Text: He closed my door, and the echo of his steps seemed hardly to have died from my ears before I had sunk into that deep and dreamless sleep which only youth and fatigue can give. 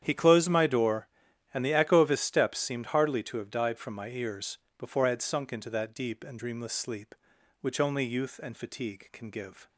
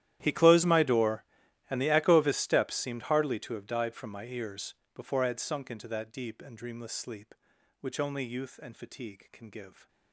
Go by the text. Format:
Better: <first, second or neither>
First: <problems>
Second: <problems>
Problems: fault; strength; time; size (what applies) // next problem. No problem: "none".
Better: first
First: starts louder than the rest; strong; until 1.0 s; 9 dB // pauses between "ears" and "before"; slight; at 4.5 s; 0.20 s long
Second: gets quieter; strong; throughout; 22 dB // starts louder than the rest; strong; until 1.2 s; 12 dB // pauses between "ears" and "before"; slight; at 4.7 s; 0.20 s long